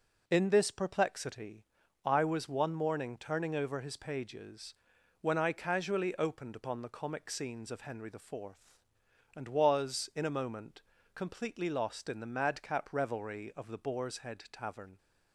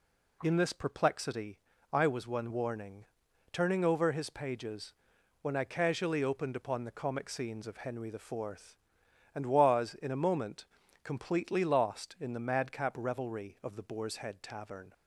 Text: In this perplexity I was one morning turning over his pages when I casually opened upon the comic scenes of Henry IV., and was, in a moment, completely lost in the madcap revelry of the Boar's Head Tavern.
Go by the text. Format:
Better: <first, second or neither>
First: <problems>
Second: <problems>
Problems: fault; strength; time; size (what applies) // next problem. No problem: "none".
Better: first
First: pauses between "perplexity" and "I"; at 1.6 s; 0.38 s long // pauses between "pages" and "when"; noticeable; at 4.7 s; 0.48 s long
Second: pauses between "perplexity" and "I"; slight; at 1.5 s; 0.34 s long // says "warning" for "morning"; at 2.5 s // pauses between "pages" and "when"; noticeable; at 4.9 s; 0.48 s long